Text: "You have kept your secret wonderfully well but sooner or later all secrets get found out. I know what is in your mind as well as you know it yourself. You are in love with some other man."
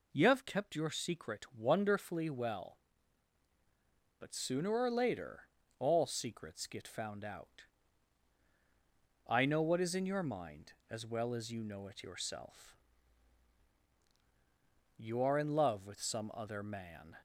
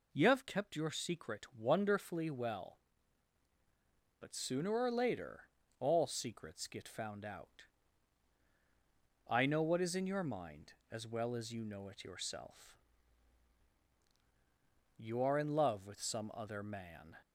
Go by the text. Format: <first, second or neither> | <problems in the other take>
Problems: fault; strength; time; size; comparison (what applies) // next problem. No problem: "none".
neither | pauses between "later" and "all"; slight; the same in both